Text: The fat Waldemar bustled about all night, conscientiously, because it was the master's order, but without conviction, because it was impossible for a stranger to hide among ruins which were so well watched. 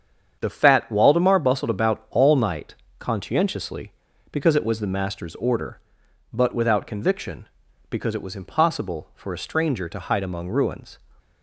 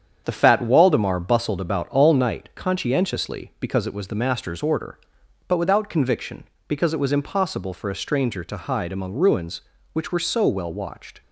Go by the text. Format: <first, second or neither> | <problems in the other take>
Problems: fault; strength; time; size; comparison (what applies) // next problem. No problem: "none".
second | starts louder than the rest; strong; until 1.4 s; 8 dB; strong in the second // stops before "which were so well watched"; at 11.2 s